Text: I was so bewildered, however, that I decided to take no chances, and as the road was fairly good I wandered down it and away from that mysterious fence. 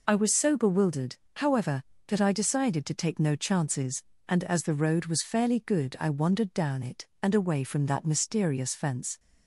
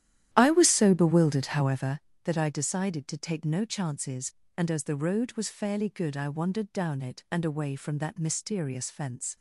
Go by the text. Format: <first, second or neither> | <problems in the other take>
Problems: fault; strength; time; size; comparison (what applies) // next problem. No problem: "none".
first | starts louder than the rest; strong; until 2.1 s; 12 dB